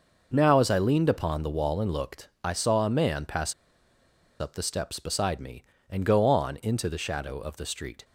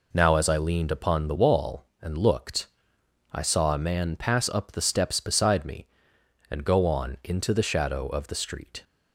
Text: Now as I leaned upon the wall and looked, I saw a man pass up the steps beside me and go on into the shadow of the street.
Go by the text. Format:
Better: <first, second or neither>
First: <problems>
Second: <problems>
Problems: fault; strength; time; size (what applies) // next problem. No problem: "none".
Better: second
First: pauses between "pass" and "up"; noticeable; at 3.5 s; 0.86 s long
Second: none